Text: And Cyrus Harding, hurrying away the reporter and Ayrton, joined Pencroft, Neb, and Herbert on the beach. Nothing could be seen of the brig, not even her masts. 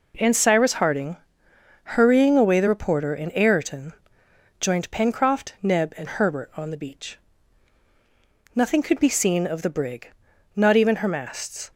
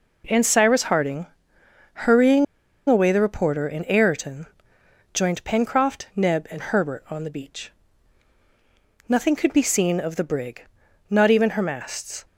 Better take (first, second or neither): first